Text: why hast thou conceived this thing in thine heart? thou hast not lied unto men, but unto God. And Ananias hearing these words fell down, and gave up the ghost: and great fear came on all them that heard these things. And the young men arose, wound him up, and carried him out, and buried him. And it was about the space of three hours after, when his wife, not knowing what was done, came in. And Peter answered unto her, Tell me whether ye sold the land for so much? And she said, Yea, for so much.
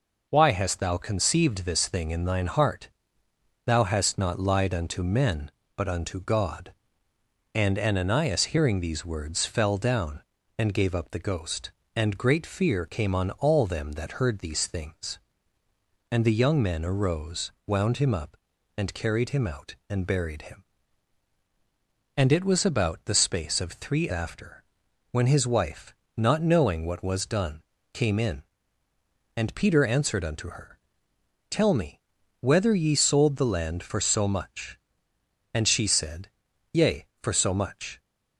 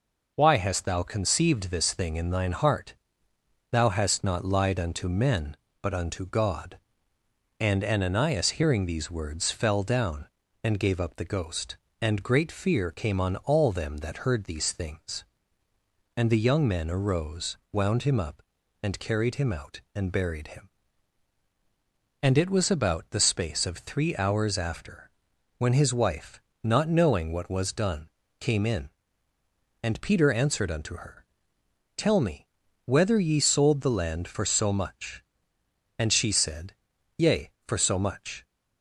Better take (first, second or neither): second